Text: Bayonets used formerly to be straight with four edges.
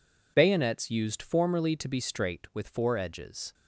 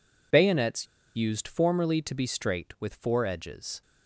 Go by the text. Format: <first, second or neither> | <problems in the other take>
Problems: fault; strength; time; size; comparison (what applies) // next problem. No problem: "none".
first | pauses between "Bayonets" and "used"; slight; at 0.8 s; 0.31 s long